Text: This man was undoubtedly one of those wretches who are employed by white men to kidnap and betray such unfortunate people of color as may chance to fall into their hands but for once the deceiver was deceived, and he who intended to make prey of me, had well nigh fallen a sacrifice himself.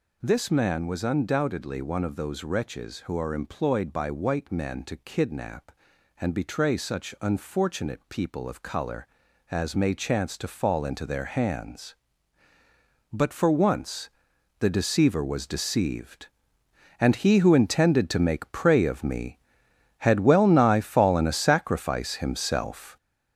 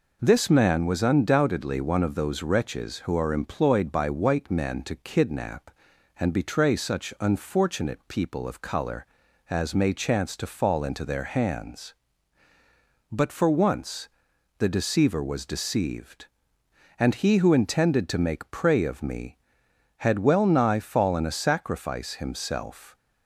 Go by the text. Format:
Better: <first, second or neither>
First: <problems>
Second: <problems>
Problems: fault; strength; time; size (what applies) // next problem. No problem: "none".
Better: second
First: gets louder; throughout; 6.5 dB // pauses between "once" and "the"; noticeable; at 14.0 s; 0.52 s long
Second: pauses between "once" and "the"; noticeable; at 14.0 s; 0.52 s long